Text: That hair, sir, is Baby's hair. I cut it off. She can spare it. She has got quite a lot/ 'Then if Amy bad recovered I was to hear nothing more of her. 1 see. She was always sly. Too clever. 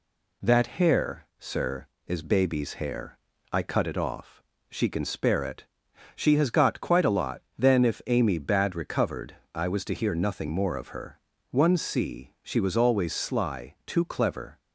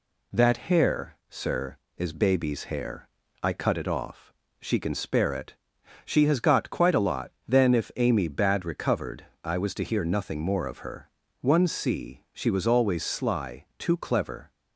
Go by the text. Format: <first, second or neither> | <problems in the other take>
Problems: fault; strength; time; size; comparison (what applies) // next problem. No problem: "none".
neither | pauses between "recovered" and "I"; slight; the same in both